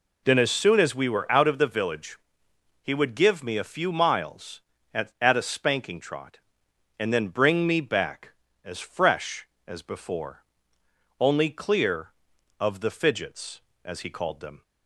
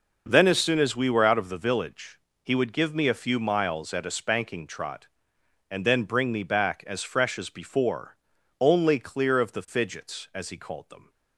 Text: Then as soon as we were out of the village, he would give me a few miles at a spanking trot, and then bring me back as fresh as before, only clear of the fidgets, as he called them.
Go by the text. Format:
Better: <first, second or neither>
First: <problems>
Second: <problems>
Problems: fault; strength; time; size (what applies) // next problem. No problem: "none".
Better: second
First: says "at" twice; at 5.1 s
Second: none